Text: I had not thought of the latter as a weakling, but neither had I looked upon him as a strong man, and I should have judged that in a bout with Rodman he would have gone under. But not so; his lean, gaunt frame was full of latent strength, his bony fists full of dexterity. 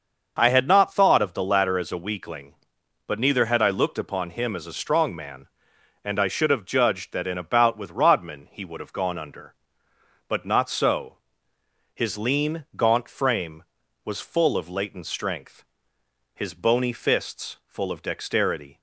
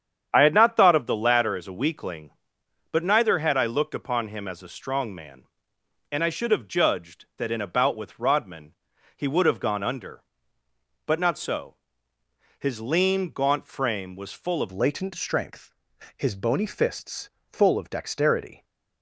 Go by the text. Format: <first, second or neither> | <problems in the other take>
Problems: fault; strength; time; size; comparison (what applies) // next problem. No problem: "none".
first | starts louder than the rest; strong; until 1.3 s; 8.5 dB; also in the first // pauses between "Rodman" and "he"; noticeable; at 8.7 s; 0.46 s long // changes voice at "latent"; from 14.7 s on; 3.9 s long // pauses between "fists" and "full"; slight; at 17.2 s; 0.20 s long